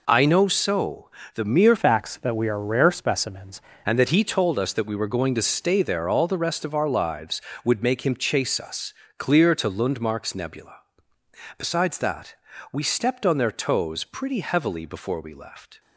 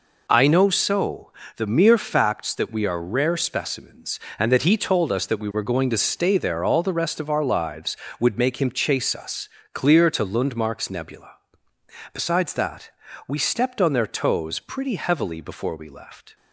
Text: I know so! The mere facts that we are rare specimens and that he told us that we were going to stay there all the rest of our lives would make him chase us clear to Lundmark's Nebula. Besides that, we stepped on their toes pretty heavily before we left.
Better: second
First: changes voice from "facts" to "specimens"; from 1.7 to 3.6 s; 1.9 s long // pauses between "us" and "clear"; slight; at 8.9 s; 0.24 s long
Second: pauses between "us" and "clear"; slight; at 9.4 s; 0.24 s long

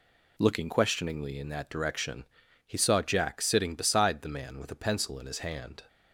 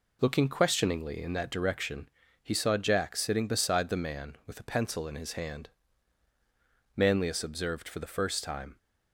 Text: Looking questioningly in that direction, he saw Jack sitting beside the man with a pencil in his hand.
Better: first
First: none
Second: goes on to say "Manlius observed for the first time"; strong; from 6.9 s on; 1.8 s long

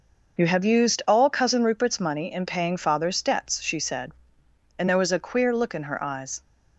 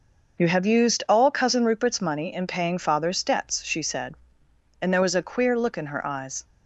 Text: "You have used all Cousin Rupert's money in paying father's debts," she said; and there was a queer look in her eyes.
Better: neither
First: none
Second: none

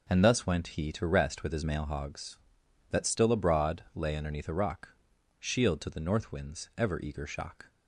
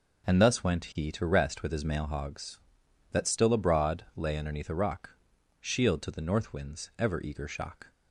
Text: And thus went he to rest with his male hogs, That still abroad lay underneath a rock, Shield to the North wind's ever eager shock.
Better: neither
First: none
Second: none

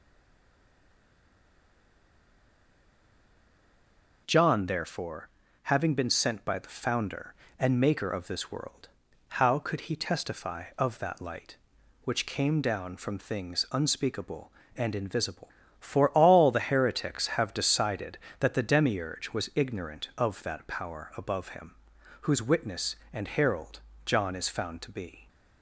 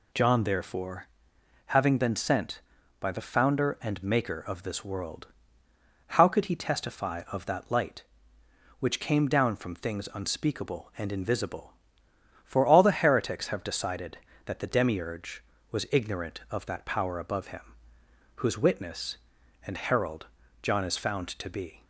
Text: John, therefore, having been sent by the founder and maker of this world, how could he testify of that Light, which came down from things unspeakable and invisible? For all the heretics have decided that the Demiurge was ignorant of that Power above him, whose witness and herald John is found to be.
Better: second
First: stays silent before the first word; strong; until 4.2 s; 4.2 s long // pauses between "herald" and "John"; slight; at 23.7 s; 0.26 s long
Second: pauses between "herald" and "John"; slight; at 20.2 s; 0.36 s long

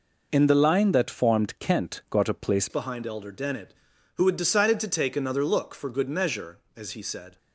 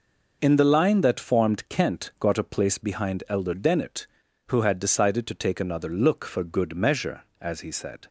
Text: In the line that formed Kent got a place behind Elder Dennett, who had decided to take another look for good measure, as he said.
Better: second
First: changes voice at "behind"; from 2.6 s on; 4.7 s long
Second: none

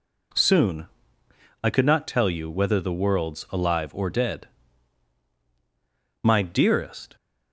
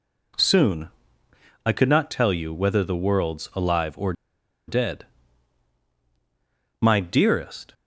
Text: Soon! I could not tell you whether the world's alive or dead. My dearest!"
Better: first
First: none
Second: pauses between "or" and "dead"; noticeable; at 4.1 s; 0.55 s long

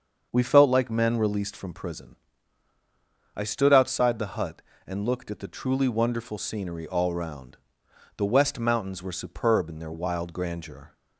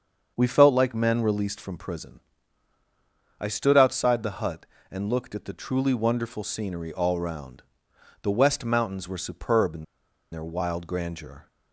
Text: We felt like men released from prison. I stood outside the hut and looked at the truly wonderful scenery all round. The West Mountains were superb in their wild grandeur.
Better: first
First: starts louder than the rest; until 1.3 s; 7 dB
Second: starts louder than the rest; until 1.3 s; 7 dB // pauses between "in" and "their"; noticeable; at 9.8 s; 0.48 s long

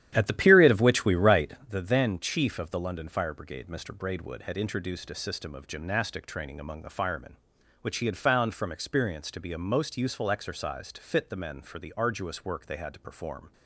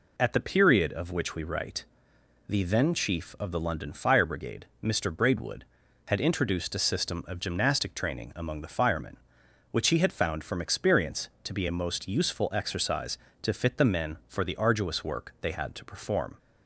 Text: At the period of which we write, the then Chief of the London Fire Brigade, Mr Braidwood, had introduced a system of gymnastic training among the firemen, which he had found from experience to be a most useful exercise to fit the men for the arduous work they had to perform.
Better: second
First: starts louder than the rest; strong; until 1.7 s; 11 dB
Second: none

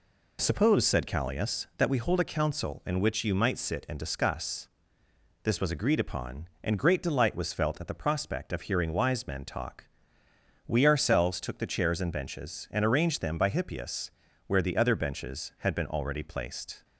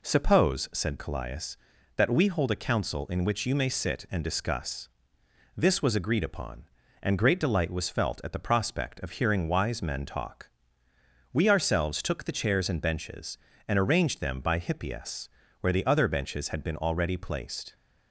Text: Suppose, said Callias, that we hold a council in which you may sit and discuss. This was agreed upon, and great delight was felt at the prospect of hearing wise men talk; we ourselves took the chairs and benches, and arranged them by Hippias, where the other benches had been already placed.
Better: second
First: says "might" for "may"; at 3.3 s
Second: none

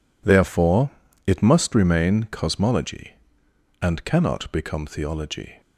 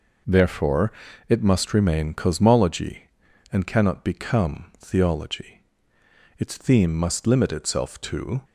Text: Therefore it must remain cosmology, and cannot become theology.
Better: first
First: pauses between "Therefore" and "it"; at 0.8 s; 0.38 s long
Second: pauses between "Therefore" and "it"; at 0.9 s; 0.38 s long // goes on to say "Its theme must limit itself to"; strong; from 6.3 s on; 2.0 s long

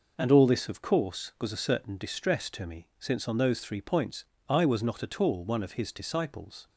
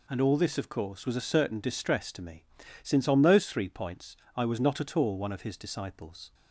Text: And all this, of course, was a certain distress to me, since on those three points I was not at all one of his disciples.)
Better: neither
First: pauses between "points" and "I"; slight; at 4.2 s; 0.24 s long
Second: pauses between "points" and "I"; slight; at 4.1 s; 0.20 s long

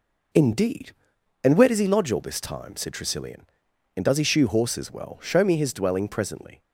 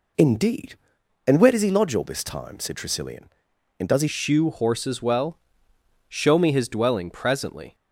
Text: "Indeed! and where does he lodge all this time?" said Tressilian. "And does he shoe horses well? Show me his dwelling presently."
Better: first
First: none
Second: changes voice at "shoe"; from 4.0 s on; 3.7 s long

